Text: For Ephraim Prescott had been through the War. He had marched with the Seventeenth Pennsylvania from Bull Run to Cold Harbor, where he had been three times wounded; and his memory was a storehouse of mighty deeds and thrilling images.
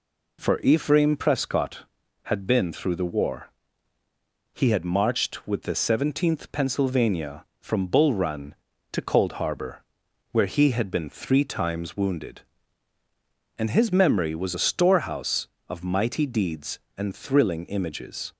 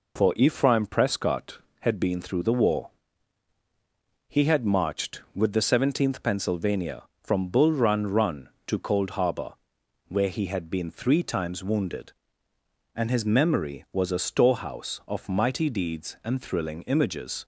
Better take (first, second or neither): first